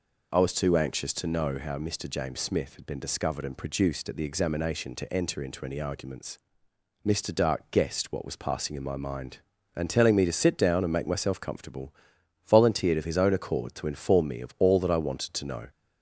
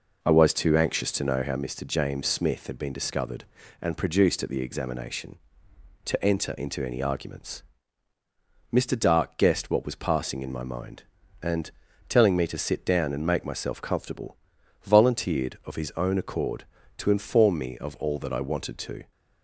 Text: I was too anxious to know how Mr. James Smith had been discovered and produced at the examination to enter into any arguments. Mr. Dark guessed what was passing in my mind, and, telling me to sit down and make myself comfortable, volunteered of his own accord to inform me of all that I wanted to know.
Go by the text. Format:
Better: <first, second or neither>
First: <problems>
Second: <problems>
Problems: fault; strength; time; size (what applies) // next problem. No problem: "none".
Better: first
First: none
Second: stops before "know"; at 19.1 s